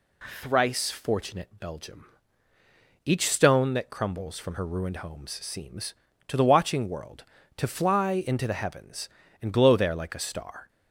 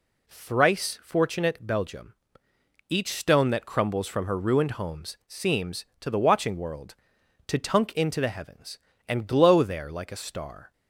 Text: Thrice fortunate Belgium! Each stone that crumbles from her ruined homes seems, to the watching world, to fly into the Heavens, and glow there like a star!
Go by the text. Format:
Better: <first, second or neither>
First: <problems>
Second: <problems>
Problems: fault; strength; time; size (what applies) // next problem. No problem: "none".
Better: first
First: none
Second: says "tunk" for "fly"; at 7.5 s